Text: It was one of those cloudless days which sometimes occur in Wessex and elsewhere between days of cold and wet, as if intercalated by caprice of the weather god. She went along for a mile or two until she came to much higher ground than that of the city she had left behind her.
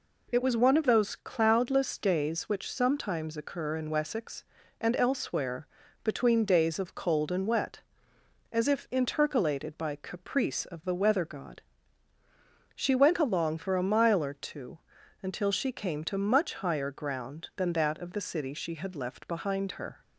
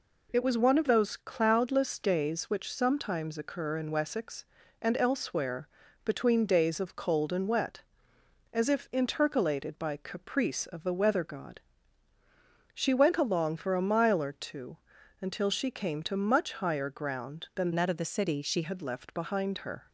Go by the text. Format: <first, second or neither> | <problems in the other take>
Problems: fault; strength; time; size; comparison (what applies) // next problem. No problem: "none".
first | pauses between "elsewhere" and "between"; at 5.6 s; 0.38 s long; also in the first // pauses between "two" and "until"; at 14.7 s; 0.44 s long; also in the first // changes voice from "that" to "she"; from 17.7 to 18.6 s; 0.9 s long